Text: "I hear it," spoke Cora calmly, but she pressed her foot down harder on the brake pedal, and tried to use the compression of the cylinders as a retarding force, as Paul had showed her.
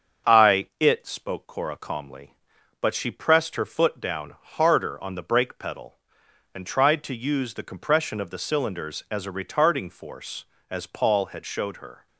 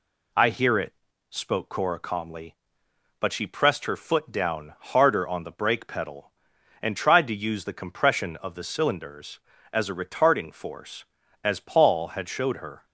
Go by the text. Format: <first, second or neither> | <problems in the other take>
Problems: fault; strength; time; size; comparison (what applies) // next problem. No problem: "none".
second | starts louder than the rest; strong; until 1.3 s; 7 dB // skips "hear"; at 0.7 s